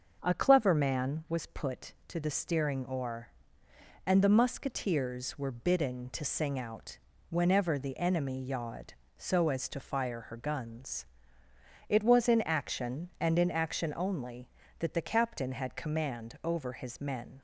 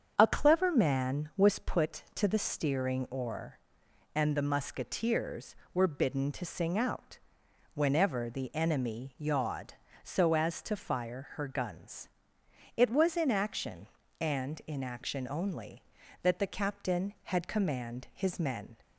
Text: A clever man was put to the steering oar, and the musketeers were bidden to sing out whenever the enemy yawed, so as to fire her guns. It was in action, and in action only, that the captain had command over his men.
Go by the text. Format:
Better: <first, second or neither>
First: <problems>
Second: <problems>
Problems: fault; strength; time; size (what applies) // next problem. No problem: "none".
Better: first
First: starts louder than the rest; until 1.2 s; 6.5 dB // pauses between "out" and "whenever"; slight; at 6.9 s; 0.32 s long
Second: starts louder than the rest; strong; until 1.1 s; 7.5 dB // pauses between "out" and "whenever"; noticeable; at 7.1 s; 0.56 s long // skips "over"; at 18.1 s